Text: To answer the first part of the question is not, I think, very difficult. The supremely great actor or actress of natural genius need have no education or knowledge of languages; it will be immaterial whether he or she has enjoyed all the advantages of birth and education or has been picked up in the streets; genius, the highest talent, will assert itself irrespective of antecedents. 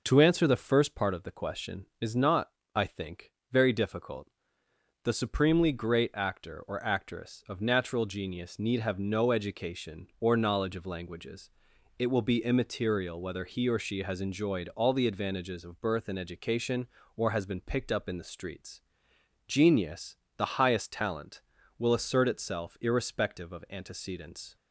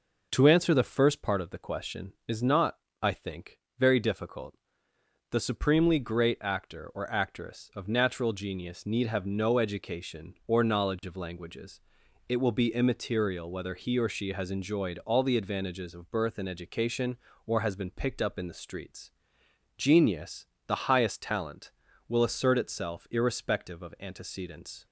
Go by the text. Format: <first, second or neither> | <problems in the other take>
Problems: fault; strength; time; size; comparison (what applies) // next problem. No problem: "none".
neither | none